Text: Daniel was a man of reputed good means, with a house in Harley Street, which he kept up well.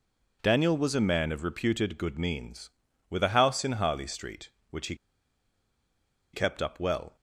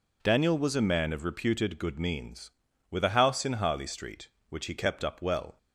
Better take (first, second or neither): second